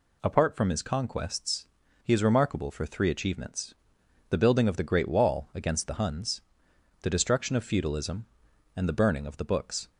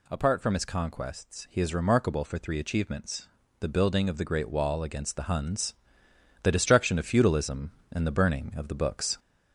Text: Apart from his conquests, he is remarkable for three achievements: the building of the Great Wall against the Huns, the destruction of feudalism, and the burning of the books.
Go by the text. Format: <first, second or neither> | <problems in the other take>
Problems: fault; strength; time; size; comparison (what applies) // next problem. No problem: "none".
first | gets louder; slight; throughout; 2.5 dB